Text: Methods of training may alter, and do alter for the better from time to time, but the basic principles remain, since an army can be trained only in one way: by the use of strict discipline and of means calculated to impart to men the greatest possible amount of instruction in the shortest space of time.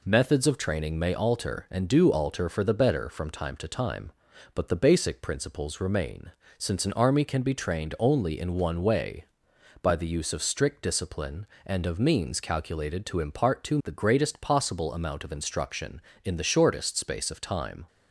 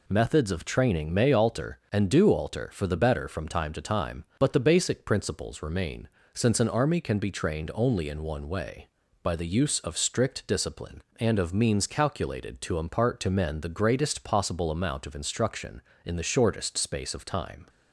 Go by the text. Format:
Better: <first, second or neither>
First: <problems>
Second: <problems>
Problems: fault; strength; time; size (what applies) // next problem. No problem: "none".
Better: second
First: skips "men"; at 13.8 s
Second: none